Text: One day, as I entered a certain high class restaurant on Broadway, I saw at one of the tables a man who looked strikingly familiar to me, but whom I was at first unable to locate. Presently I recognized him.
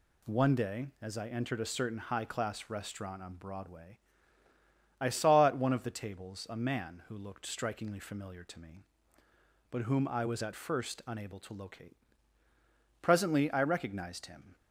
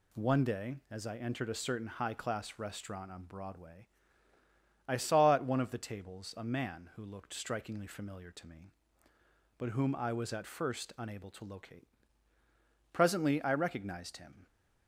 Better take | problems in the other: neither | none

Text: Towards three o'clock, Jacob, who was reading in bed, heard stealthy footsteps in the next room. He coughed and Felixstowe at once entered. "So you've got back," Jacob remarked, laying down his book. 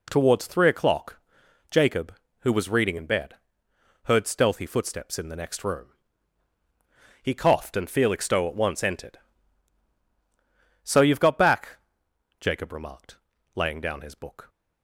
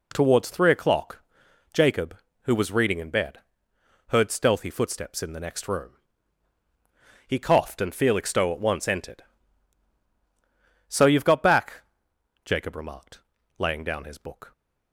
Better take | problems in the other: neither | none

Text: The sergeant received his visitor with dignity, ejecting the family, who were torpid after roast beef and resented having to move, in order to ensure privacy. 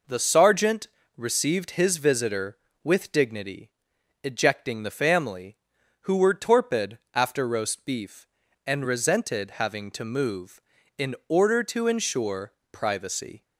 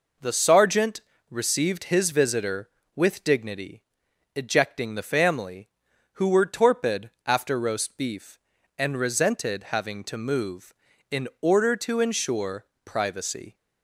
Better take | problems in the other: neither | pauses between "sergeant" and "received"; slight; the same in both // pauses between "torpid" and "after"; slight; the same in both // pauses between "ensure" and "privacy"; slight; the same in both

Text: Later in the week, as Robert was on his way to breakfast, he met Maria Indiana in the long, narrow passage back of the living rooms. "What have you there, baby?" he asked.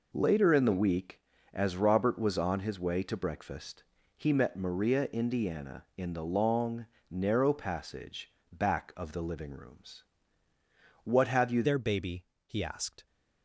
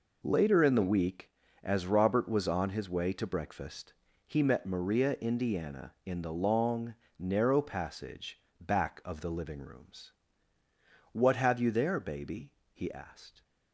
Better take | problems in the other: second | pauses between "passage" and "back"; slight; at 8.3 s; 0.20 s long; slight in the second // changes voice at "there"; from 11.6 s on; 1.4 s long

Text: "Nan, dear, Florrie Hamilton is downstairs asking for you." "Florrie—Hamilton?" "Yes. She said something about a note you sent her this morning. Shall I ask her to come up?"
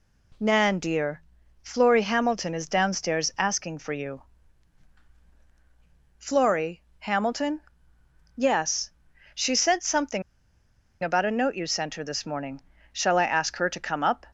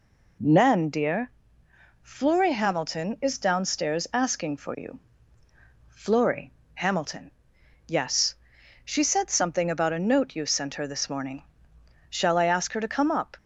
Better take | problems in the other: second | pauses between "something" and "about"; noticeable; at 10.2 s; 0.81 s long

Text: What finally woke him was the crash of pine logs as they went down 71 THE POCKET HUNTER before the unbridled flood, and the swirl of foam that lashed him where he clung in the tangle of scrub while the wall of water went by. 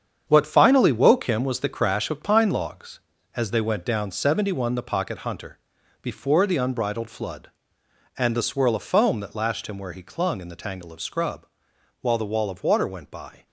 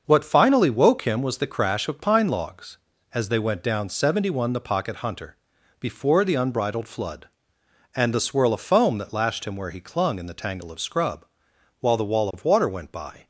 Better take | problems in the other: second | gets quieter; strong; throughout; 9 dB // starts louder than the rest; strong; until 1.2 s; 7.5 dB; also in the second // pauses between "HUNTER" and "before"; at 5.5 s; 0.44 s long; also in the second // pauses between "scrub" and "while"; noticeable; at 11.4 s; 0.54 s long; noticeable in the second

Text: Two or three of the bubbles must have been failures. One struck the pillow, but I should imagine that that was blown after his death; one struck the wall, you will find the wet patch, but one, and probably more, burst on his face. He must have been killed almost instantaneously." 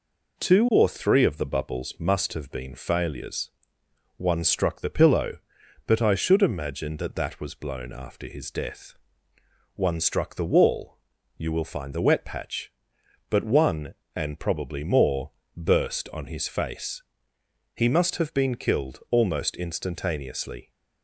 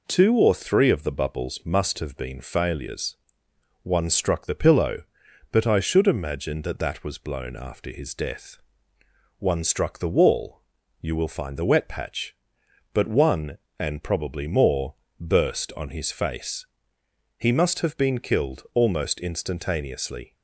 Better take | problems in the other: neither | none

